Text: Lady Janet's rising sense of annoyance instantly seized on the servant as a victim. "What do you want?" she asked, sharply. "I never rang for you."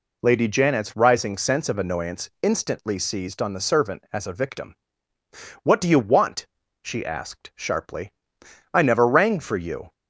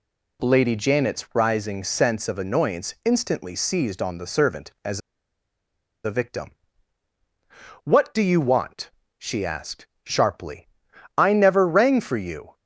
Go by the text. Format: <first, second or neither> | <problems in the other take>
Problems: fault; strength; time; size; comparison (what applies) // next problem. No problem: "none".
first | pauses between "as" and "a"; at 4.9 s; 1.0 s long